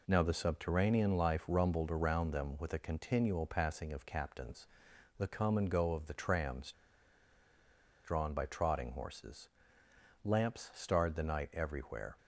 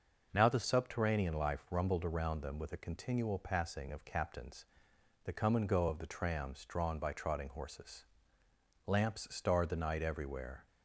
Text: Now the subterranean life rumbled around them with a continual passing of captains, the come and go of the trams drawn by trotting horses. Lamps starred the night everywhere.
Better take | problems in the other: second | pauses between "trams" and "drawn"; strong; at 6.7 s; 1.3 s long

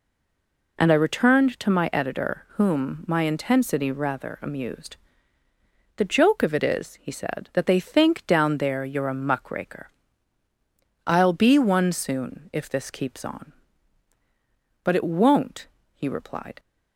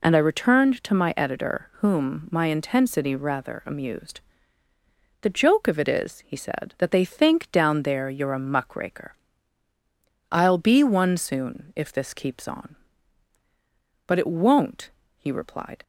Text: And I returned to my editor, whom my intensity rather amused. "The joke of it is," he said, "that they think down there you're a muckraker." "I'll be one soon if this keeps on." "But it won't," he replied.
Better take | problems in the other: second | stays silent before the first word; slight; until 0.7 s; 0.7 s long

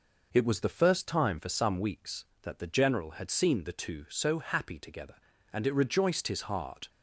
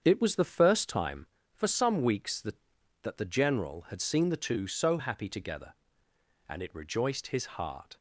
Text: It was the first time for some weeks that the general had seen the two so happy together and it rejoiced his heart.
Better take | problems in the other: first | starts louder than the rest; strong; until 1.0 s; 7.5 dB // says "that" twice; at 3.0 s

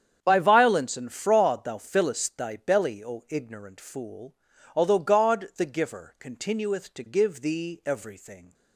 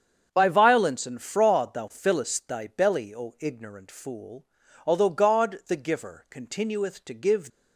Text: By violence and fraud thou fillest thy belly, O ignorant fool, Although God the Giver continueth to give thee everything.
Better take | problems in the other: first | starts louder than the rest; strong; until 1.3 s; 7.5 dB; strong in the first // stops before "thee everything"; at 7.5 s

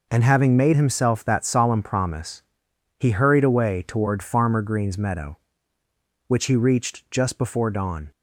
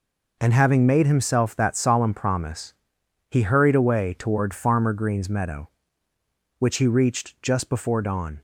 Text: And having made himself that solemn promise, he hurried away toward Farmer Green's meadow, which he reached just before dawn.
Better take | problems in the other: neither | none

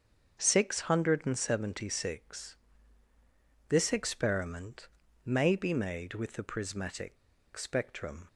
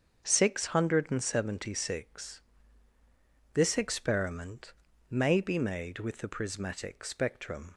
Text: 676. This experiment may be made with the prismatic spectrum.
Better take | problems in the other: second | starts louder than the rest; until 1.4 s; 7 dB; also in the second // pauses between "experiment" and "may"; at 4.8 s; 0.38 s long; also in the second // pauses between "prismatic" and "spectrum"; at 7.1 s; 0.40 s long

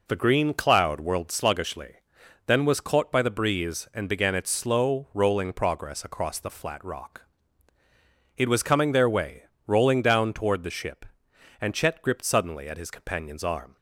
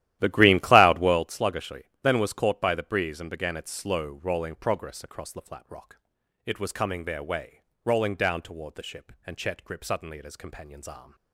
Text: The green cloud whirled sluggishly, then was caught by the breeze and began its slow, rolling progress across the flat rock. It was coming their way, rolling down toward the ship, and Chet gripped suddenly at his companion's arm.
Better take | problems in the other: first | starts louder than the rest; strong; until 1.3 s; 13.5 dB

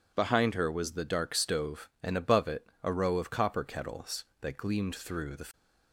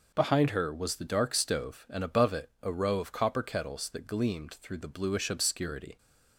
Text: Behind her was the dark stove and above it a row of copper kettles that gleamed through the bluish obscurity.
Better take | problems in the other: second | pauses between "it" and "a"; slight; at 2.6 s; 0.16 s long // stops before "bluish obscurity"; at 5.5 s

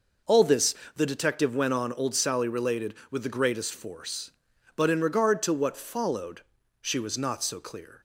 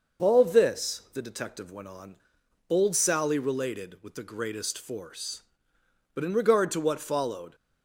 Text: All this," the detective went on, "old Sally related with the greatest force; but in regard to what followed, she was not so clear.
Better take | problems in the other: first | starts louder than the rest; noticeable; until 1.3 s; 6 dB // stops before "she was not so clear"; at 7.5 s

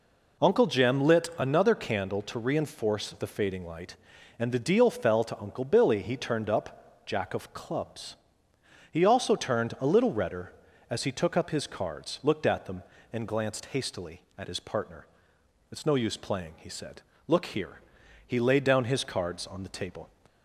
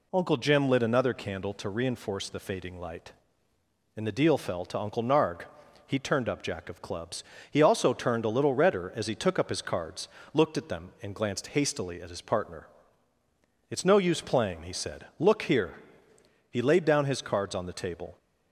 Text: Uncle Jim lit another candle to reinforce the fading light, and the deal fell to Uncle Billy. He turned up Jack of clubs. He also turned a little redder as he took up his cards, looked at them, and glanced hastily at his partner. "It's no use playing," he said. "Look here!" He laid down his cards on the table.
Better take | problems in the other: first | says "Narg" for "Billy"; at 5.0 s

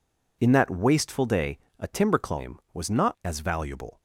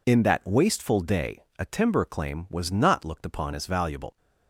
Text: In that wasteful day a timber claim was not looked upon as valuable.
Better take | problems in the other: second | pauses between "day" and "a"; slight; at 1.5 s; 0.22 s long // skips "looked upon"; at 3.1 s

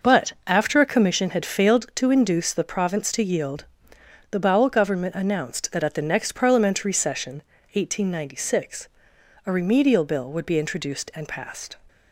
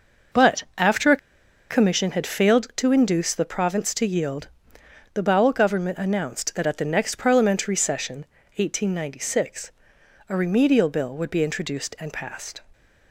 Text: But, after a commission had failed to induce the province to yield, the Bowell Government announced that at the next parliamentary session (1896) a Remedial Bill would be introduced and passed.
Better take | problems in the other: first | pauses between "a" and "commission"; noticeable; at 1.1 s; 0.53 s long

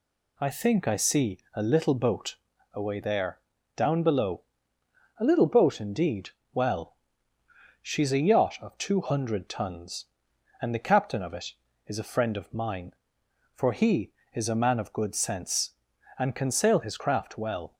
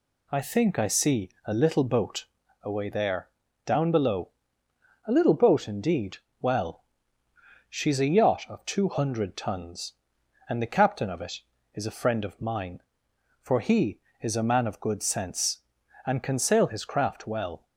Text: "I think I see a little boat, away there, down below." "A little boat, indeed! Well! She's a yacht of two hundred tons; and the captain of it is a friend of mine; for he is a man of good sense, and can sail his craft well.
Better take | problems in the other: neither | pauses between "see" and "a"; slight; the same in both

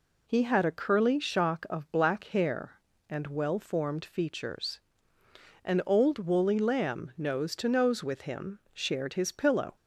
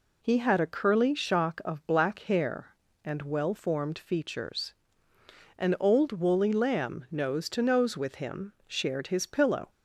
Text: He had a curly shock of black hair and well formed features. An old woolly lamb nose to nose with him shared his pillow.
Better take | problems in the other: neither | pauses between "him" and "shared"; slight; the same in both

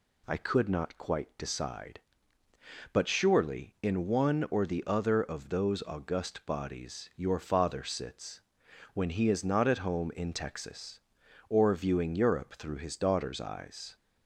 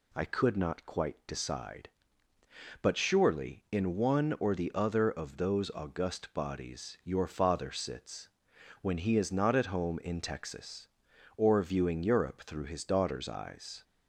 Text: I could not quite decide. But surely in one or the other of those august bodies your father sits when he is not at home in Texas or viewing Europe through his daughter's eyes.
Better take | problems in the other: neither | pauses between "sits" and "when"; noticeable; the same in both

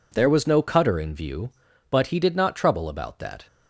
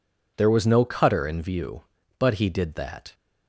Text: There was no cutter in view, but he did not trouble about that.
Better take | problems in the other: first | skips "not trouble about"; at 2.7 s

